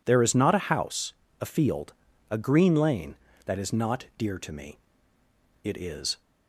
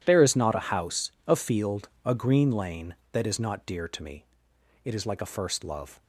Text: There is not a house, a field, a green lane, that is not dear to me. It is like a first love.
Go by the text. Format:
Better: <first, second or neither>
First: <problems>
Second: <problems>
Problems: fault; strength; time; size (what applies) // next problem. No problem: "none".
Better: second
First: stops before "like a first love"; at 6.2 s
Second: none